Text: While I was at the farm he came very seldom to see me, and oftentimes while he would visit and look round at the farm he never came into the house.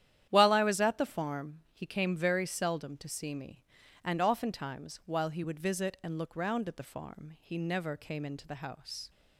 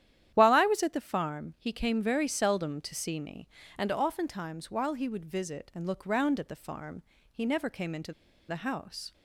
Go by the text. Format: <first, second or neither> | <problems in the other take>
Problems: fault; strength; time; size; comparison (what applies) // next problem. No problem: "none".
first | starts louder than the rest; strong; until 1.3 s; 10.5 dB; strong in the first // pauses between "farm" and "he"; slight; at 7.0 s; 0.26 s long // pauses between "into" and "the"; at 8.1 s; 0.37 s long